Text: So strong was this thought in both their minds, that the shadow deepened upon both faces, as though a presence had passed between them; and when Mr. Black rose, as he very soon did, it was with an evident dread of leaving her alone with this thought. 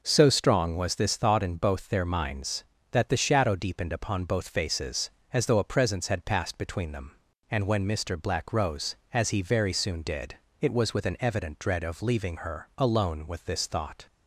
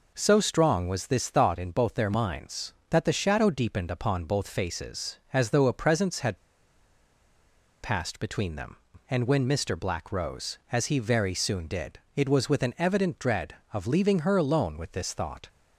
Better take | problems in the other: first | pauses between "had" and "passed"; strong; at 6.3 s; 1.4 s long

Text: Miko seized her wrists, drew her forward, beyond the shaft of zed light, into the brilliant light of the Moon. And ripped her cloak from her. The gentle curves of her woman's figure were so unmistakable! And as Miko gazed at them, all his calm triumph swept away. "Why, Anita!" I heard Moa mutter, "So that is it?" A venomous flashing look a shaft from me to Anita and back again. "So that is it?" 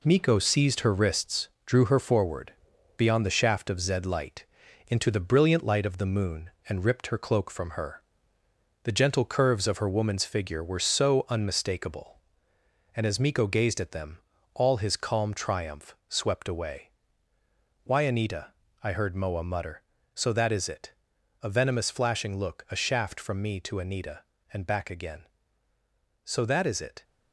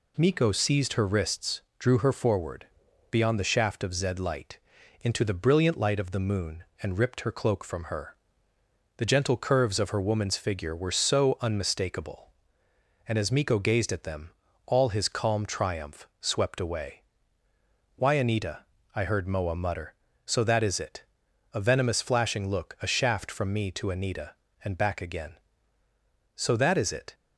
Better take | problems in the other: second | gets quieter; noticeable; throughout; 6 dB

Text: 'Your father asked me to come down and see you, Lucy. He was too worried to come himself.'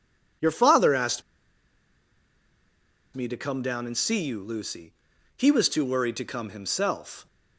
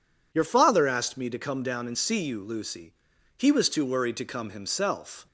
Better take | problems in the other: second | pauses between "asked" and "me"; strong; at 1.2 s; 1.9 s long

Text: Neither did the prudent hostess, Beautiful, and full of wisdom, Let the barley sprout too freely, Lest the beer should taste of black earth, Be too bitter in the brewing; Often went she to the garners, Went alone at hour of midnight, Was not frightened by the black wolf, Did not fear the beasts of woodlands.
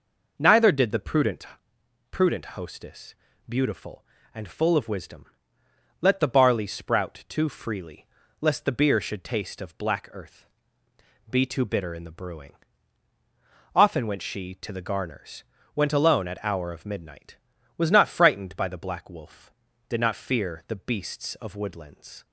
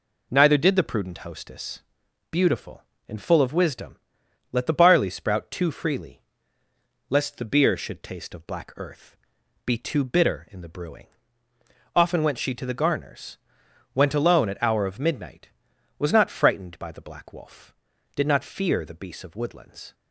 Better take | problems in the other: second | says "prudent" twice; at 2.1 s

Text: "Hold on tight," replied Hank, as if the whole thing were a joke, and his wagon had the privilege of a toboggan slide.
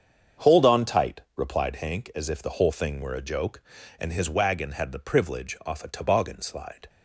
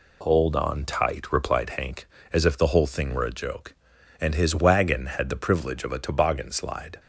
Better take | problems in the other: second | starts louder than the rest; strong; until 1.5 s; 7 dB // says "off" for "of"; at 5.6 s

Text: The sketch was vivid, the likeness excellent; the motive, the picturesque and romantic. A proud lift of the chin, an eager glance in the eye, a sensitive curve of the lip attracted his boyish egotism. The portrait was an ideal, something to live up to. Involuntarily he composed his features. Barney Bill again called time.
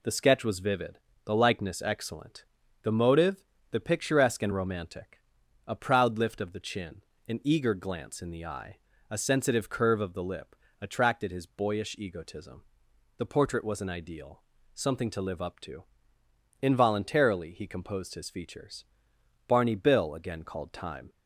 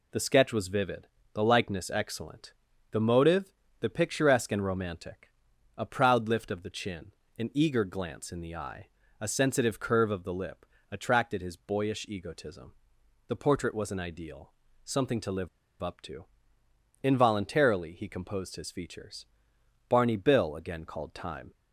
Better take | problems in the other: first | pauses between "lip" and "attracted"; slight; at 10.6 s; 0.26 s long; slight in the first // pauses between "live" and "up"; slight; at 15.4 s; 0.34 s long

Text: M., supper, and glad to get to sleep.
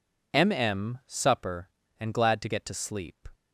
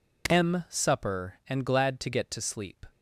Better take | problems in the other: second | says "M" twice; at 0.5 s

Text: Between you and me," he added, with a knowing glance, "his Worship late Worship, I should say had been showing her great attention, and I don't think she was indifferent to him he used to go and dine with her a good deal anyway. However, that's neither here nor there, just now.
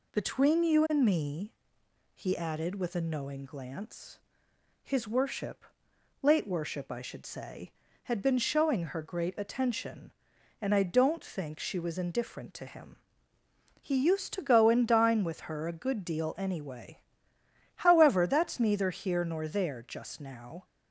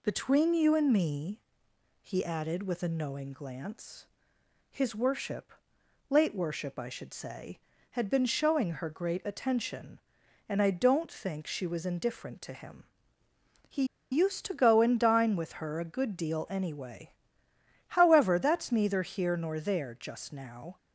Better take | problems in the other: first | pauses between "Worship" and "late"; noticeable; at 5.5 s; 0.56 s long; noticeable in the first // pauses between "him" and "he"; noticeable; at 12.8 s; 0.84 s long; noticeable in the first // pauses between "he" and "used"; slight; at 13.8 s; 0.27 s long

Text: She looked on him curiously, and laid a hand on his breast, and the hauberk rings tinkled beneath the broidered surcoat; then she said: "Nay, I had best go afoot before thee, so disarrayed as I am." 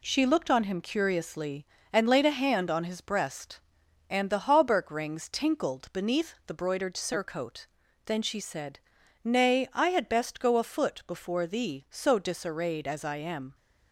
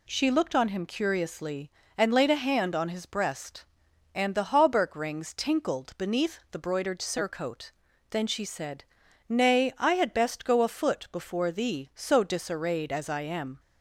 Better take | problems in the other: second | gets quieter; noticeable; throughout; 4.5 dB

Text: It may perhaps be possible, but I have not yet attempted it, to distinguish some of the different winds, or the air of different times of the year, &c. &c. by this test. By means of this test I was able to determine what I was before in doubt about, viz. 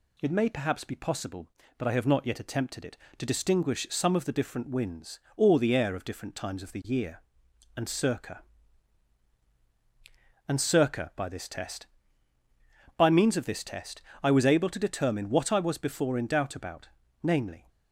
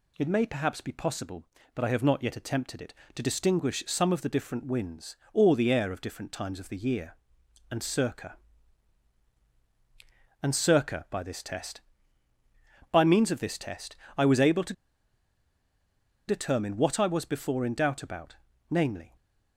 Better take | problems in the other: first | pauses between "test" and "I"; slight; at 13.9 s; 0.20 s long; slight in the first // pauses between "to" and "determine"; strong; at 14.7 s; 1.5 s long

